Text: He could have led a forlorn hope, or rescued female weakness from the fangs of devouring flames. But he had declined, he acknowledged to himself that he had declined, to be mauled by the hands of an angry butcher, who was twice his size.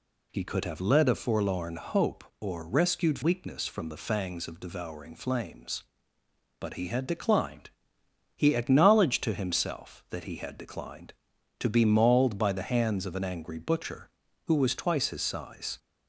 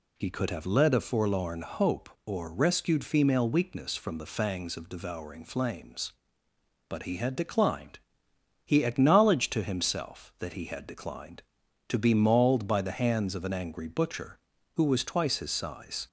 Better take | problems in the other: second | skips "female"; at 3.2 s

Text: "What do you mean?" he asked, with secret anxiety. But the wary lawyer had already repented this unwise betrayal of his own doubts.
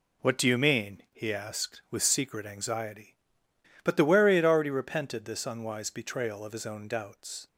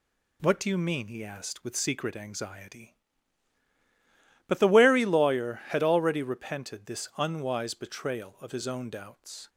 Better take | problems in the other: second | skips "lawyer"; at 4.3 s

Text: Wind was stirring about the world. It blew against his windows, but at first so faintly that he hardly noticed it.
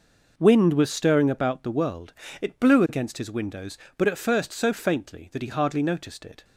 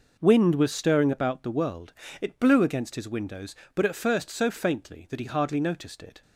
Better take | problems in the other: neither | none

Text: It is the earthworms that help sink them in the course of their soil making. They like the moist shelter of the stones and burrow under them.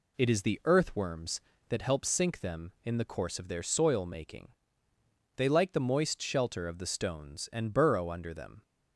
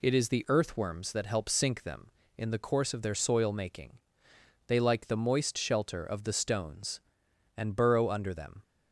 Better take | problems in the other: neither | none

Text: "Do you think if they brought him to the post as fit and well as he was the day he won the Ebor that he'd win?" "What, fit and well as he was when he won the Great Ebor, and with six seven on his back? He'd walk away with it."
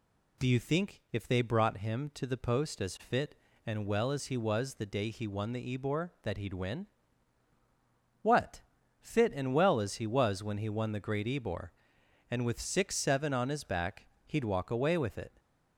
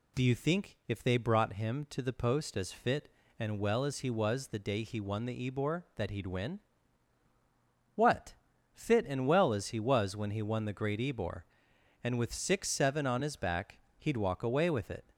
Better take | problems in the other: neither | none

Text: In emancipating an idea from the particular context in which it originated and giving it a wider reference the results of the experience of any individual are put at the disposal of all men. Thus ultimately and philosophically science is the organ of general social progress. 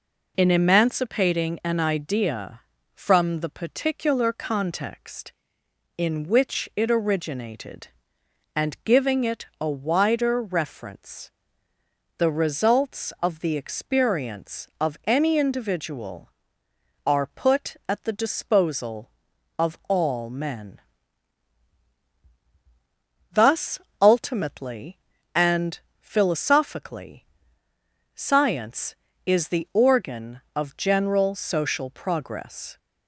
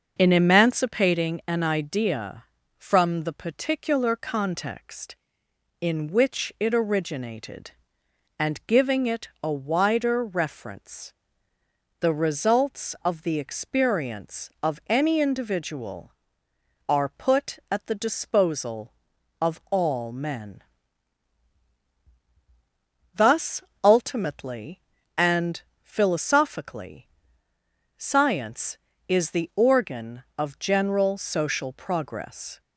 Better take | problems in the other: first | starts louder than the rest; until 1.2 s; 6 dB // pauses between "reference" and "the"; noticeable; at 11.1 s; 0.88 s long; noticeable in the first // pauses between "Thus" and "ultimately"; slight; at 23.6 s; 0.24 s long; slight in the first // pauses between "and" and "philosophically"; slight; at 25.6 s; 0.22 s long; slight in the first // pauses between "philosophically" and "science"; noticeable; at 27.0 s; 0.92 s long; noticeable in the first

